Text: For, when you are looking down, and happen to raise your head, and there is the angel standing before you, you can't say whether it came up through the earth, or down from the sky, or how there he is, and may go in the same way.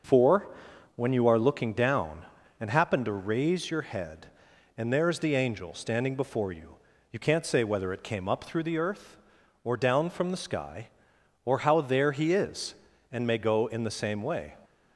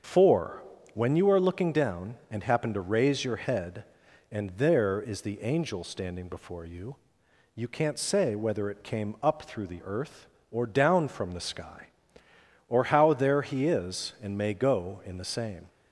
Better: first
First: starts louder than the rest; until 1.5 s; 6 dB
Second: starts louder than the rest; until 1.3 s; 7 dB // stops before "way"; at 15.6 s

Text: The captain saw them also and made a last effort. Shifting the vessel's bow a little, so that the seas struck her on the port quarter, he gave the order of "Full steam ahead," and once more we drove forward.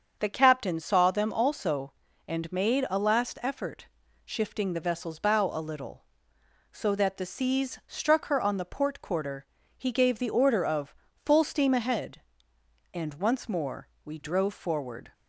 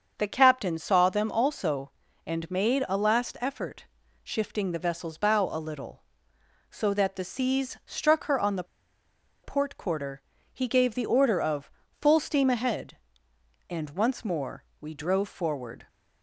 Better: first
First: starts louder than the rest; until 1.2 s; 6.5 dB // pauses between "of" and "Full"; slight; at 10.9 s; 0.28 s long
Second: starts louder than the rest; until 1.1 s; 6.5 dB // pauses between "the" and "port"; noticeable; at 8.6 s; 0.79 s long // pauses between "of" and "Full"; slight; at 11.7 s; 0.28 s long

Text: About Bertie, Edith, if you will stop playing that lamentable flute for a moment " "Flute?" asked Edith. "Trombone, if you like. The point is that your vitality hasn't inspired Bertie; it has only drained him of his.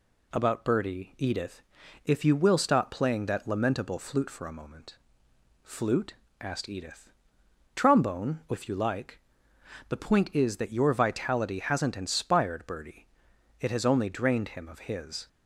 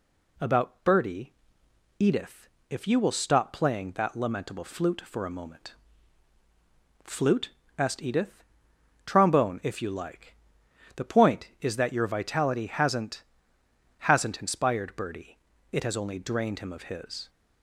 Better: first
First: none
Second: says "hasn't" twice; at 14.0 s

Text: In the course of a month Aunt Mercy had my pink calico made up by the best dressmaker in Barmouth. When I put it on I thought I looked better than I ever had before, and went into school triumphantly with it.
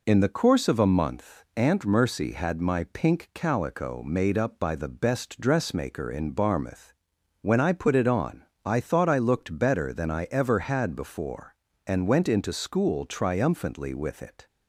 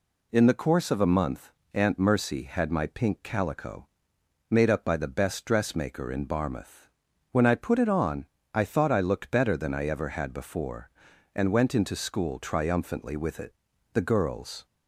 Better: first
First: pauses between "on" and "I"; slight; at 8.4 s; 0.24 s long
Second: pauses between "month" and "Aunt"; slight; at 1.4 s; 0.24 s long // pauses between "calico" and "made"; noticeable; at 3.8 s; 0.60 s long // pauses between "on" and "I"; slight; at 8.2 s; 0.28 s long // goes on to say "The girls"; noticeable; from 13.9 s on; 0.72 s long

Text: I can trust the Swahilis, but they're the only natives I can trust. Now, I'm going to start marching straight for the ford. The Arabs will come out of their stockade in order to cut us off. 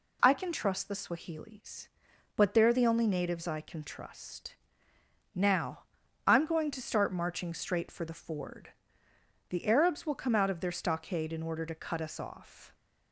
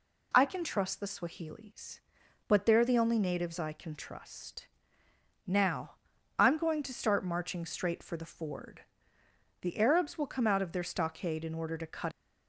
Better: first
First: none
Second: stops before "us off"; at 12.1 s

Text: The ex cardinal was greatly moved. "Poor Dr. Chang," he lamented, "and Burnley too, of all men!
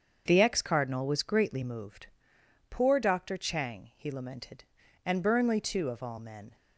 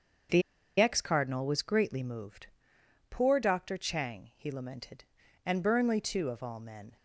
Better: first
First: starts louder than the rest; until 1.2 s; 7 dB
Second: starts louder than the rest; noticeable; until 1.6 s; 6 dB // pauses between "The" and "ex"; at 0.4 s; 0.38 s long

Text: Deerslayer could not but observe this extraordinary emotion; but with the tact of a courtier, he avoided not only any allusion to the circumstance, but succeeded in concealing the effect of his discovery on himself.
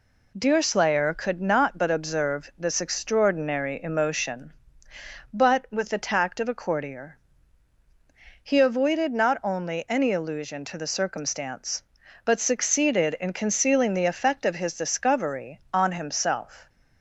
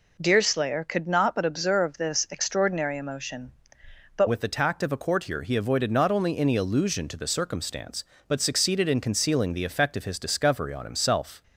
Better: first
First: none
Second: changes voice at "with"; from 4.2 s on; 7.2 s long

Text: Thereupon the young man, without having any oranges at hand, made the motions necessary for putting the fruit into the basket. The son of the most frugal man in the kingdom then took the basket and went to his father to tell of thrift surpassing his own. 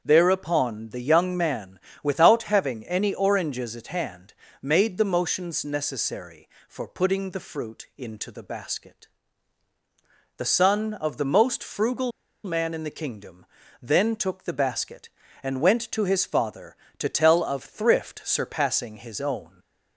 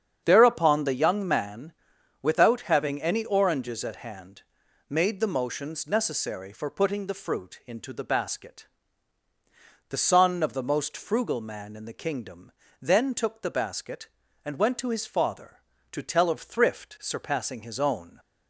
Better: second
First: starts louder than the rest; until 1.0 s; 6.5 dB // pauses between "frugal" and "man"; slight; at 12.1 s; 0.33 s long // pauses between "kingdom" and "then"; slight; at 13.4 s; 0.36 s long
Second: starts louder than the rest; strong; until 1.2 s; 8 dB // pauses between "kingdom" and "then"; slight; at 12.5 s; 0.28 s long

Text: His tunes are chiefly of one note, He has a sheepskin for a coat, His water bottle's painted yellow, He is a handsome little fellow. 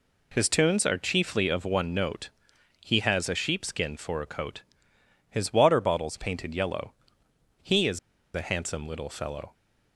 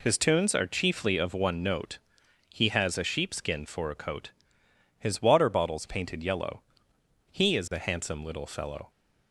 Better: second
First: pauses between "is" and "a"; slight; at 7.9 s; 0.36 s long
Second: none

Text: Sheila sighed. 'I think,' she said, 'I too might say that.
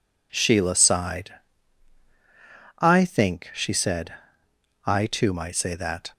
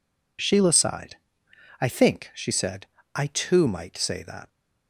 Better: neither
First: none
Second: none

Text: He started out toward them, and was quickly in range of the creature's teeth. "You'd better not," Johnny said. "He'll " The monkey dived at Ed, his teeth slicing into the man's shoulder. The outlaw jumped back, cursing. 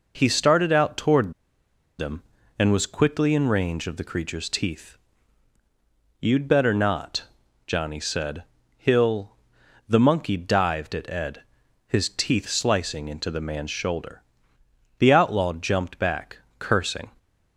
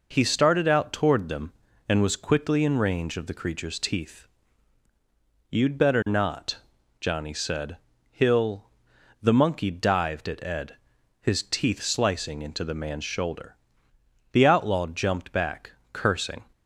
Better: second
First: pauses between "toward" and "them"; noticeable; at 1.3 s; 0.66 s long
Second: none

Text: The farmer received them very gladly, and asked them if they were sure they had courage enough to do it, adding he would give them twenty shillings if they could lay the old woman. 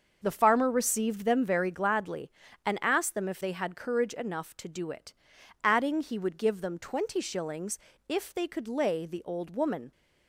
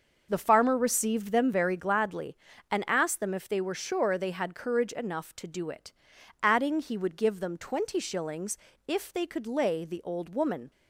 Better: second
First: starts louder than the rest; until 1.2 s; 6.5 dB // skips "they were sure"; at 3.4 s // pauses between "shillings" and "if"; slight; at 7.7 s; 0.28 s long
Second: starts louder than the rest; noticeable; until 1.3 s; 6 dB // pauses between "shillings" and "if"; slight; at 8.5 s; 0.28 s long

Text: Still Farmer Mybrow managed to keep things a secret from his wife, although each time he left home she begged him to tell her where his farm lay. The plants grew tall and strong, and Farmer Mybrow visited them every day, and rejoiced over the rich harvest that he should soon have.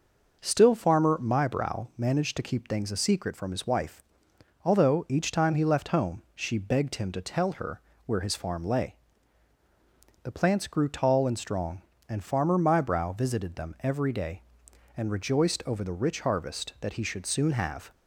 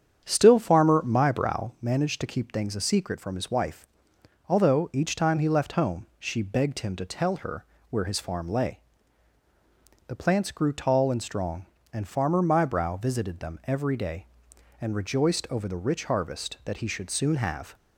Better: first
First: pauses between "her" and "where"; slight; at 7.8 s; 0.24 s long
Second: starts louder than the rest; strong; until 1.8 s; 8.5 dB // pauses between "her" and "where"; slight; at 7.6 s; 0.24 s long

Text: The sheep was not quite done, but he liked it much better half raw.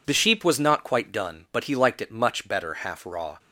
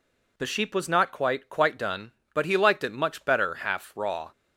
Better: first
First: none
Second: says "quite" twice; at 1.4 s

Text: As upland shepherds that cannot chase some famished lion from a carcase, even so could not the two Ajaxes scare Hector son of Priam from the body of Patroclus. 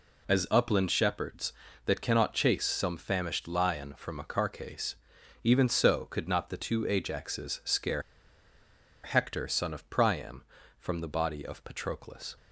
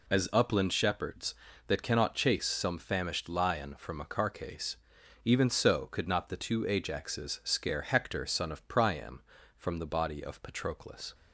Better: second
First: pauses between "scare" and "Hector"; at 8.0 s; 1.0 s long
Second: none

